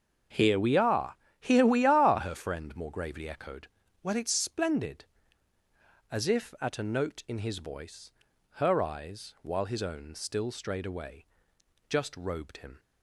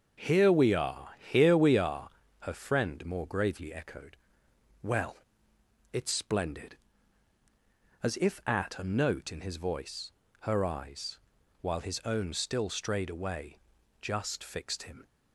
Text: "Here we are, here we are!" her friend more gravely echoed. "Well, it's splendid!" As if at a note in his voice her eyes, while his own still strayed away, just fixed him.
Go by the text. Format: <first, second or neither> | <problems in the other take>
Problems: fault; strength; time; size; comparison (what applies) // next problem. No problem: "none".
second | starts louder than the rest; until 1.5 s; 7 dB; also in the second // pauses between "voice" and "her"; at 8.1 s; 0.38 s long; slight in the second // says "robed" for "fixed"; at 12.1 s